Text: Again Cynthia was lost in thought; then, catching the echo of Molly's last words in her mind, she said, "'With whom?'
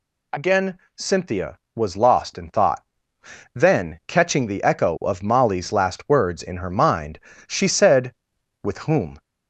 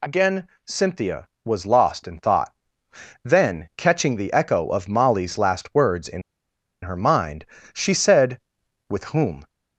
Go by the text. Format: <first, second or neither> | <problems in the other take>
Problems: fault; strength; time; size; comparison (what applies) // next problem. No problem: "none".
first | pauses between "Again" and "Cynthia"; slight; at 0.4 s; 0.20 s long; slight in the first // pauses between "in" and "her"; noticeable; at 6.2 s; 0.61 s long